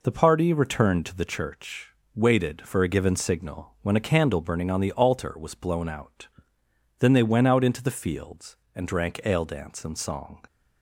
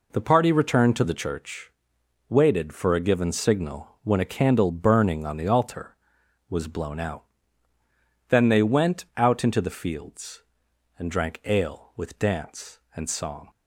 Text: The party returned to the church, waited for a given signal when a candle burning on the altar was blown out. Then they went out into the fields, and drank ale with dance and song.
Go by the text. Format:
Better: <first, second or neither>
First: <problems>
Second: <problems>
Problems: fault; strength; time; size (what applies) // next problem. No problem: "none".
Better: second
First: skips "with"; at 9.4 s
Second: none